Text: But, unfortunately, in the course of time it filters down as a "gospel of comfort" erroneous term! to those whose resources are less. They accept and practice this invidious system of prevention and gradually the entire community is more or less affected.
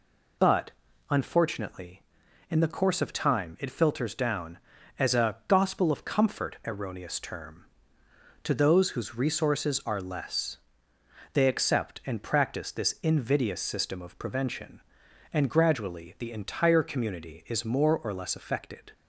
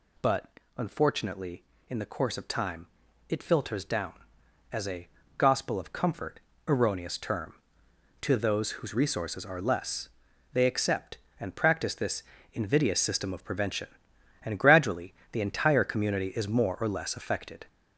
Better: first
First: none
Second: gets louder; noticeable; throughout; 5 dB // pauses between "time" and "it"; at 2.8 s; 0.42 s long // pauses between "a" and "gospel"; slight; at 5.0 s; 0.30 s long // pauses between "comfort" and "erroneous"; slight; at 6.3 s; 0.28 s long // pauses between "this" and "invidious"; slight; at 12.2 s; 0.28 s long // pauses between "gradually" and "the"; slight; at 15.1 s; 0.20 s long

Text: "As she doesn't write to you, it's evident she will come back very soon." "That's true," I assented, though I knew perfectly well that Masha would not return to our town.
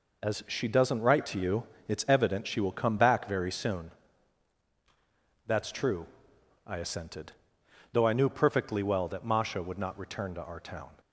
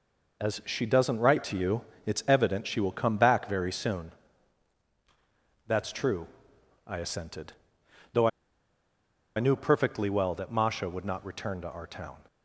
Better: first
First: none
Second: pauses between "though" and "I"; at 8.2 s; 1.0 s long

